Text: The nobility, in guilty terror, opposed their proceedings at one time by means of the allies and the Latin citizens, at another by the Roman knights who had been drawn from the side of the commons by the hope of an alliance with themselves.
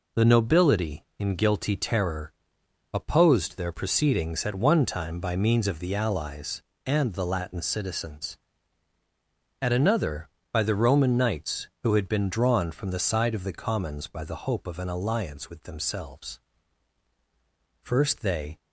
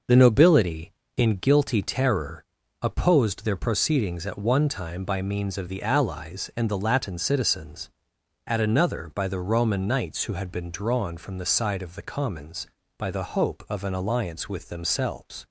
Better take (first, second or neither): second